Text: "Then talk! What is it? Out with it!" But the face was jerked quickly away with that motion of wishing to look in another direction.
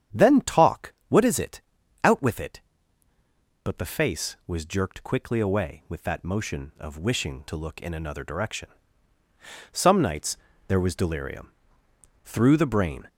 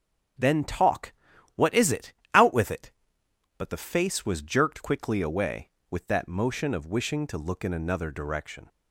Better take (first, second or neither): second